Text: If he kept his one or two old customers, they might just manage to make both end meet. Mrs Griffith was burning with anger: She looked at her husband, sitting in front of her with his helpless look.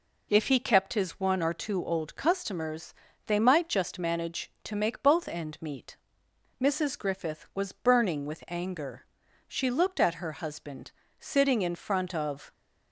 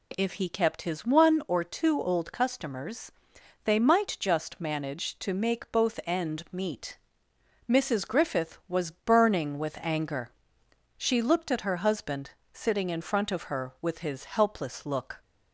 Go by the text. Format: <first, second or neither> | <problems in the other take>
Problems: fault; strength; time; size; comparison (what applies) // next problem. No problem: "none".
second | stops before "her with his helpless look"; at 12.5 s